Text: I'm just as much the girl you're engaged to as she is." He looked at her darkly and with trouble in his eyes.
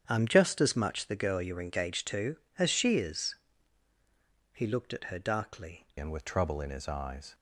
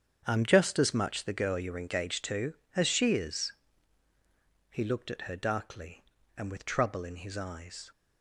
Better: second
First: starts louder than the rest; strong; until 1.0 s; 8.5 dB // changes voice at "and"; from 5.9 s on; 1.4 s long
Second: starts louder than the rest; strong; until 1.2 s; 8 dB

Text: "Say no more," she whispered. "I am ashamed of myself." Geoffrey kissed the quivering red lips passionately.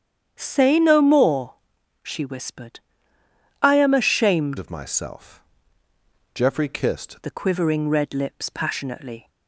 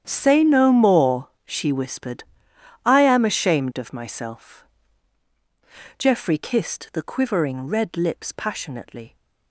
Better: second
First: starts louder than the rest; strong; until 1.3 s; 9 dB // changes voice from "of" to "kissed"; from 4.5 to 7.1 s; 2.6 s long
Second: starts louder than the rest; strong; until 1.0 s; 9 dB

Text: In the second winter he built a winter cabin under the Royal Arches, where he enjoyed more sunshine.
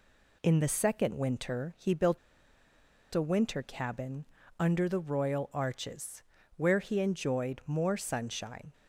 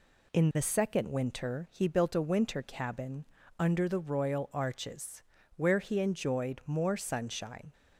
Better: second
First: pauses between "built" and "a"; noticeable; at 2.1 s; 0.96 s long // pauses between "cabin" and "under"; slight; at 4.2 s; 0.32 s long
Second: pauses between "cabin" and "under"; slight; at 3.2 s; 0.32 s long

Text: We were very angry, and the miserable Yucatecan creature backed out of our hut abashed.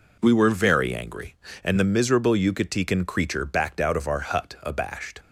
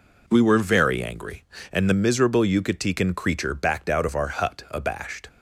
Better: neither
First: none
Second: none

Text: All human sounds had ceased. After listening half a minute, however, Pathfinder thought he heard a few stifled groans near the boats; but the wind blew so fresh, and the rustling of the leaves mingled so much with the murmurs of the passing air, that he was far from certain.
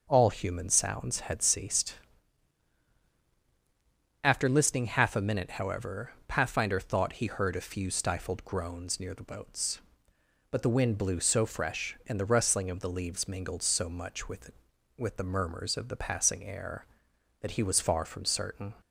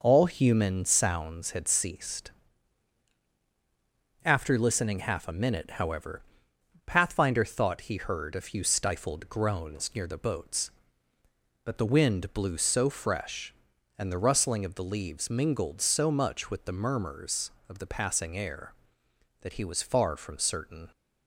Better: second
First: starts louder than the rest; until 1.0 s; 6 dB // says "with" twice; at 14.9 s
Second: none

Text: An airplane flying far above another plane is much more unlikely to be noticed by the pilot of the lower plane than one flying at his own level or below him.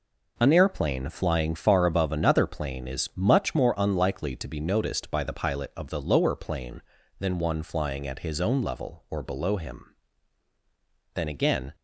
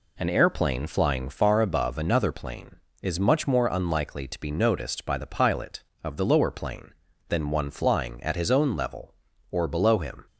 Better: second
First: goes on to say "Then again"; from 11.1 s on; 0.60 s long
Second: none

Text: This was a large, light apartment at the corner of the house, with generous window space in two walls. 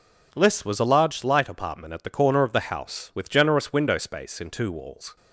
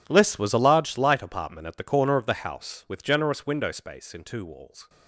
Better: first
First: none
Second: gets quieter; strong; throughout; 19 dB

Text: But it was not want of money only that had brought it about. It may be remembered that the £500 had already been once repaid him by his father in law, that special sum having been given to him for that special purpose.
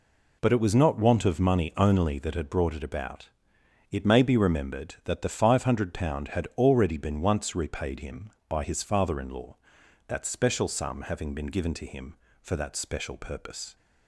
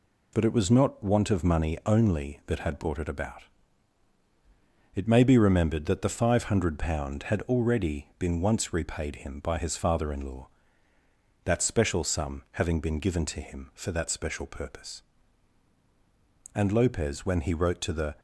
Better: first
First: none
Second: goes on to say "And Lopez when he wrote to the"; from 16.5 s on; 1.6 s long

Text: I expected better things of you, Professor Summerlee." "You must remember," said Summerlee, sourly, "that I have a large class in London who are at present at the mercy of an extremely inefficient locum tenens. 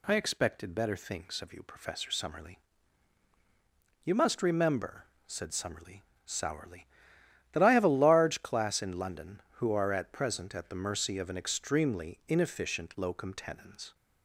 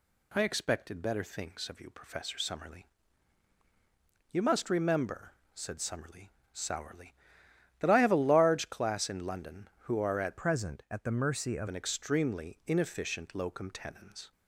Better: first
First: none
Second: changes voice from "present" to "of"; from 10.3 to 11.6 s; 1.3 s long

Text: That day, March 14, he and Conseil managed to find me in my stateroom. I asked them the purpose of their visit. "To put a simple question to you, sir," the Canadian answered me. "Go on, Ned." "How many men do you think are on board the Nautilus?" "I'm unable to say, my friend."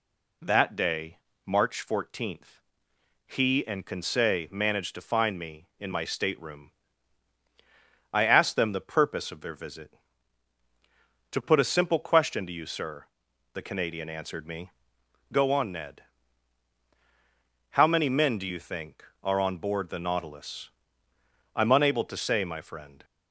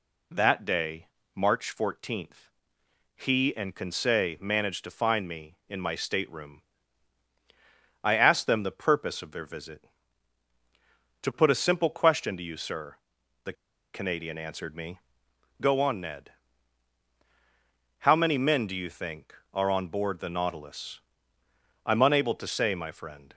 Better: first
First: none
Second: pauses between "the" and "Canadian"; at 13.5 s; 0.41 s long

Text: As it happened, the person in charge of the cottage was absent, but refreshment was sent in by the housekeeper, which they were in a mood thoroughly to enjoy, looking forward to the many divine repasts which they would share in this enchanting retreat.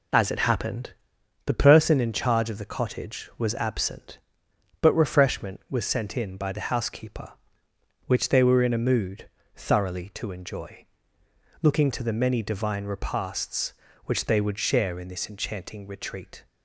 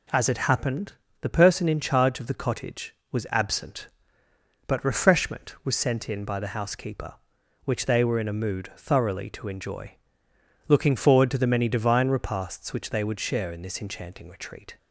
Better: second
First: pauses between "mood" and "thoroughly"; slight; at 9.2 s; 0.28 s long // skips "forward"; at 11.9 s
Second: none

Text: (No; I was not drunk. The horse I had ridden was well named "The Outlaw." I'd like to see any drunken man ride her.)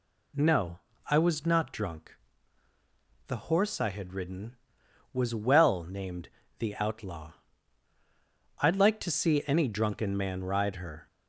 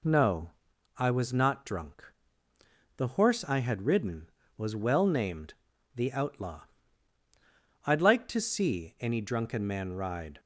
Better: first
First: pauses between "named" and "The"; slight; at 6.2 s; 0.32 s long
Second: pauses between "named" and "The"; at 5.5 s; 0.42 s long // stops before "her"; at 10.3 s

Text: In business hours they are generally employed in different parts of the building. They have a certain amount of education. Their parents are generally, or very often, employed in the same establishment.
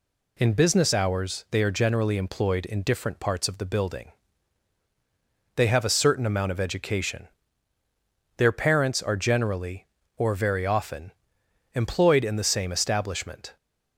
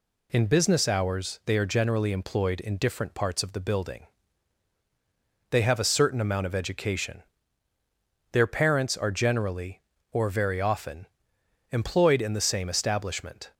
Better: neither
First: none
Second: none

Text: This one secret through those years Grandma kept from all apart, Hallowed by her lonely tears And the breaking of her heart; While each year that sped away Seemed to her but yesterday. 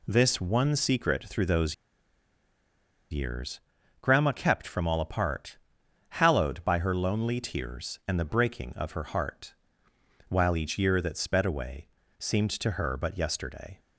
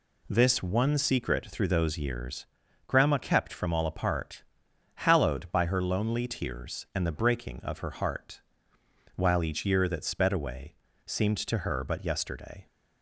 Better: second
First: pauses between "those" and "years"; strong; at 1.7 s; 1.3 s long // pauses between "years" and "Grandma"; at 3.6 s; 0.40 s long // pauses between "away" and "Seemed"; slight; at 11.8 s; 0.32 s long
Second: pauses between "years" and "Grandma"; at 2.4 s; 0.40 s long // pauses between "away" and "Seemed"; slight; at 10.7 s; 0.32 s long

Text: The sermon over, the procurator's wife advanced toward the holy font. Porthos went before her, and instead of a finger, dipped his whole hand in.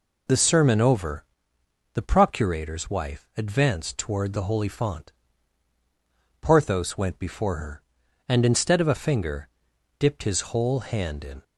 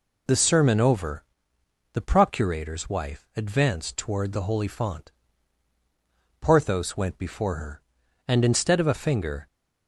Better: first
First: none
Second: stops before "dipped his whole hand in"; at 9.4 s

